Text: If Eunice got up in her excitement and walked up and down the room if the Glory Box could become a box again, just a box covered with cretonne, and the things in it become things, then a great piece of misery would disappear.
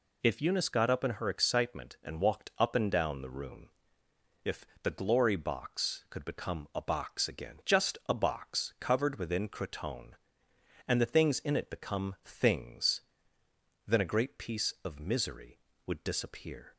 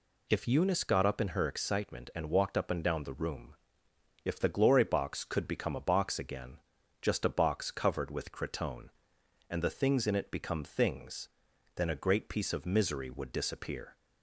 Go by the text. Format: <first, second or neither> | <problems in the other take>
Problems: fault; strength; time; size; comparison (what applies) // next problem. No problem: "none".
second | pauses between "room" and "if"; noticeable; at 3.6 s; 0.76 s long; noticeable in the second // pauses between "if" and "the"; slight; at 4.6 s; 0.16 s long // says "within" for "with"; at 9.1 s